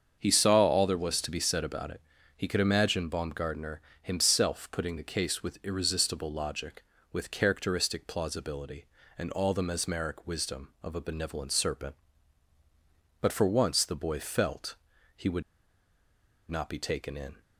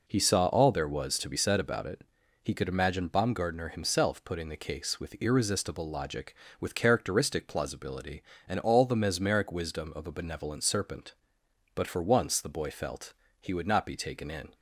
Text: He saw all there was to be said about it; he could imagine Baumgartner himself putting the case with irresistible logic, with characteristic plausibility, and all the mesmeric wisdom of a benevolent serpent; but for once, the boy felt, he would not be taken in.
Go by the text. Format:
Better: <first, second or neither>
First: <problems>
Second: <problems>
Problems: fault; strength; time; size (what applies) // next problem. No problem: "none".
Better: second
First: starts louder than the rest; until 1.2 s; 7 dB // pauses between "Baumgartner" and "himself"; slight; at 3.7 s; 0.22 s long // pauses between "would" and "not"; at 15.4 s; 1.0 s long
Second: none